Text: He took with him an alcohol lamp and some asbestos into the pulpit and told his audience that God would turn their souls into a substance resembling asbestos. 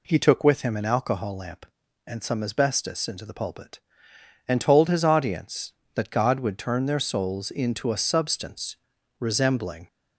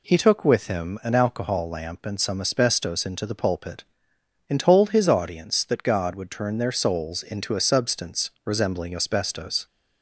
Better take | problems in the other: second | pauses between "substance" and "resembling"; at 8.7 s; 0.42 s long // stops before "asbestos"; at 9.8 s

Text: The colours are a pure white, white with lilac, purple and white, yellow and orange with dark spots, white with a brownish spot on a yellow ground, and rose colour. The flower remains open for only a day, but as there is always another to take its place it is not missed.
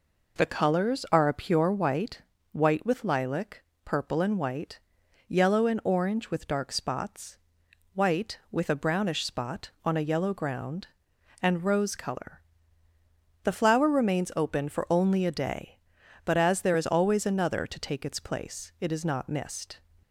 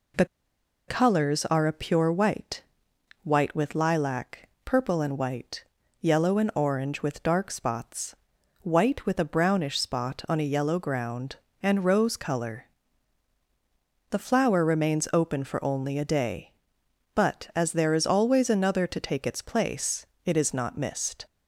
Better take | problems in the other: first | pauses between "The" and "colours"; noticeable; at 0.2 s; 0.62 s long // pauses between "place" and "it"; slight; at 20.0 s; 0.20 s long

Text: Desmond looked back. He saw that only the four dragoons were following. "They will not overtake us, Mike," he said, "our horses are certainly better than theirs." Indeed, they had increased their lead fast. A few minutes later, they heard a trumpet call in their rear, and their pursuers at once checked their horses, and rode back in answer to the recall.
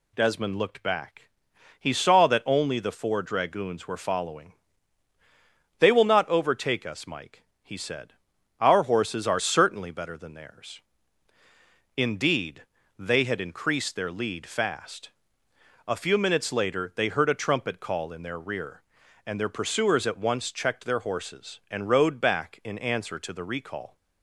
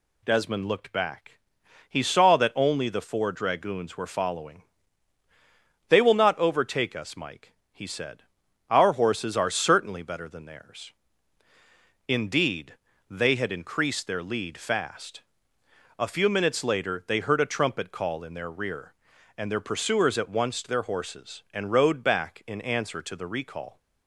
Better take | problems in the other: first | skips "checked"; at 20.6 s

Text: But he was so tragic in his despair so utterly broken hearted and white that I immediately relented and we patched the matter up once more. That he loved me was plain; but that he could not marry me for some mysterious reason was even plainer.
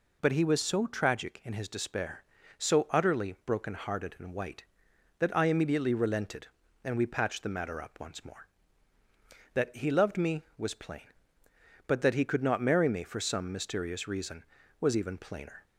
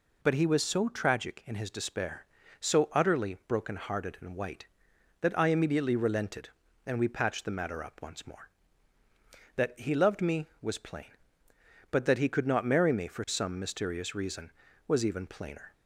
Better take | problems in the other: neither | none

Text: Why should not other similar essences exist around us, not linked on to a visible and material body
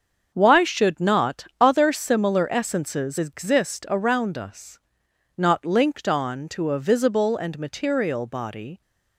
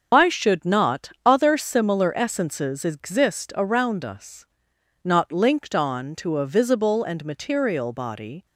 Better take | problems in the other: first | loses the start of "Why"; at 0.1 s; 135 ms // starts louder than the rest; until 1.2 s; 6.5 dB; also in the first

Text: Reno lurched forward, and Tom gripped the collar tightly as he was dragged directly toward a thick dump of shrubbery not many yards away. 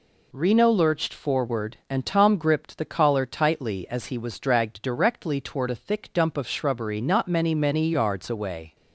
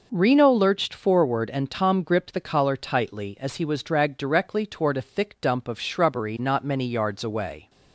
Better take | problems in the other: second | says "many" twice; at 7.5 s

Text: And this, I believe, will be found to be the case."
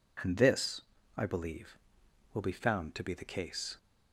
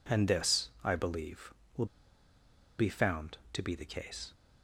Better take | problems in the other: first | pauses between "will" and "be"; noticeable; at 1.8 s; 0.93 s long

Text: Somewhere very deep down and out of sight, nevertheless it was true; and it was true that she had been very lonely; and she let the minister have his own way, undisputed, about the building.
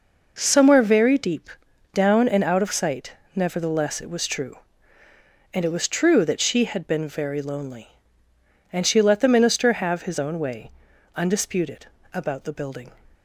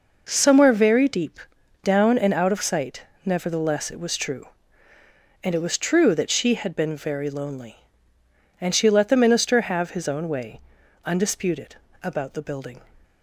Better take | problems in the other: neither | pauses between "deep" and "down"; noticeable; the same in both

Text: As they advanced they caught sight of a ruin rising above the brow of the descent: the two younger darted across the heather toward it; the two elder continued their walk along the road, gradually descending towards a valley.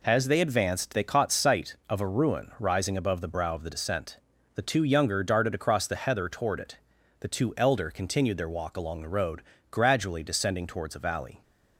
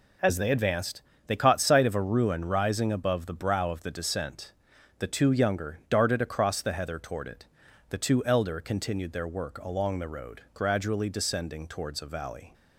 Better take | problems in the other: first | pauses between "advanced" and "they"; slight; at 1.0 s; 0.26 s long // says "work" for "walk"; at 9.2 s

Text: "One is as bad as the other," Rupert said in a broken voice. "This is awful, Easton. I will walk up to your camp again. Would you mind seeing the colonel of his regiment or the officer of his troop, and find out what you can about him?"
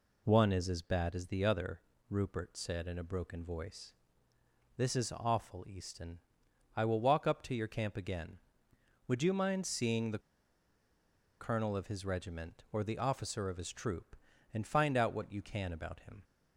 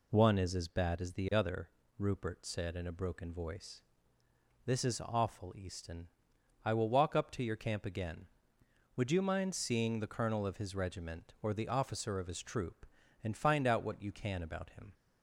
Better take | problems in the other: second | pauses between "the" and "colonel"; at 10.1 s; 1.2 s long

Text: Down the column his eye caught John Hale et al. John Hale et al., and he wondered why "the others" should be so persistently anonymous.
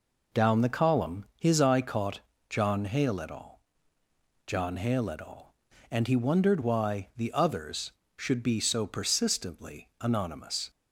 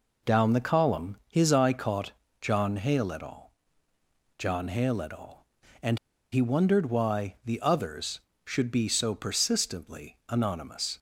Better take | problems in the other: first | pauses between "caught" and "John"; slight; at 2.1 s; 0.28 s long; slight in the first // pauses between "al" and "John"; noticeable; at 3.5 s; 0.88 s long; noticeable in the first // pauses between "and" and "he"; slight; at 5.9 s; 0.34 s long

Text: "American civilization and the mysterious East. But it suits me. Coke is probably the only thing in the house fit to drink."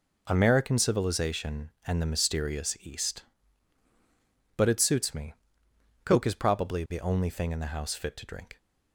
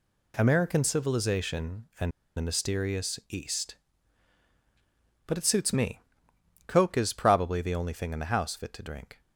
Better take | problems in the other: first | pauses between "and" and "the"; slight; at 2.1 s; 0.25 s long

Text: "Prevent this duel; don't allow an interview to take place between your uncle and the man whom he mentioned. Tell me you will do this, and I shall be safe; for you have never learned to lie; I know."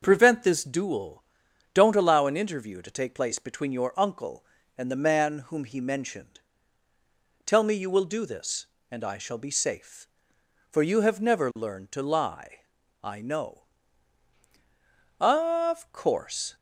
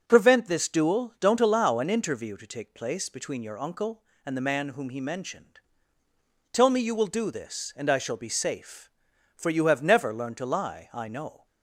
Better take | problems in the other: second | starts louder than the rest; until 1.0 s; 6.5 dB; also in the second // goes on to say "Of course"; from 15.1 s on; 1.3 s long

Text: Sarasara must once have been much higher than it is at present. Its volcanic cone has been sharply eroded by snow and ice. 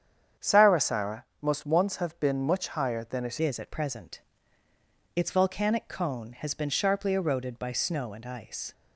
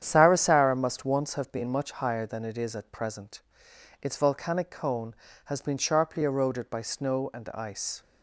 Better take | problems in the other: second | starts louder than the rest; strong; until 1.5 s; 8.5 dB; strong in the second // pauses between "Sarasara" and "must"; slight; at 1.2 s; 0.18 s long // changes voice at "is"; from 3.3 s on; 5.4 s long

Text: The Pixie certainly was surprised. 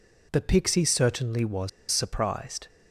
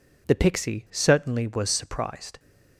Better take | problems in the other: second | pauses between "was" and "surprised"; slight; at 1.6 s; 0.22 s long

